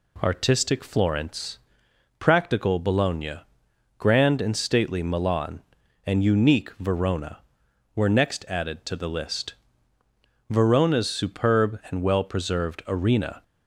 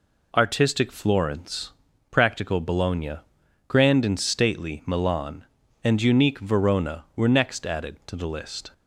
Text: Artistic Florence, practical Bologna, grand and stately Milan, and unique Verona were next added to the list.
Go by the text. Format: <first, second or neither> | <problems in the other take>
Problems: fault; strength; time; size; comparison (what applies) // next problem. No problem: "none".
second | goes on to say "Verona's superb and well preserved Arena"; strong; from 10.4 s on; 2.9 s long